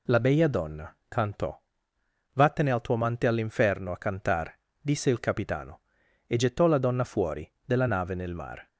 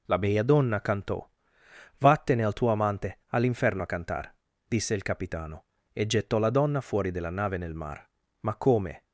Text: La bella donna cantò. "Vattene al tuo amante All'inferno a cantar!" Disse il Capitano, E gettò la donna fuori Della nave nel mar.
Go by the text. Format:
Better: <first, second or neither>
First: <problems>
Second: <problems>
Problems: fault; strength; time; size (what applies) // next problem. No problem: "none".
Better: first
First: none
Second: goes on to say "Ma come"; noticeable; from 8.3 s on; 0.64 s long